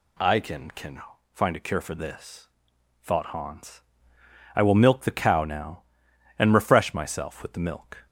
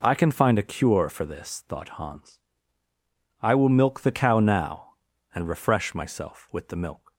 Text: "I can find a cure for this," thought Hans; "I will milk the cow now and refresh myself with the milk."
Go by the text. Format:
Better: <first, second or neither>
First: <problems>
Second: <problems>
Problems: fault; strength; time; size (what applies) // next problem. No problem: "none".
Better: second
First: says "can" twice; at 0.7 s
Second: none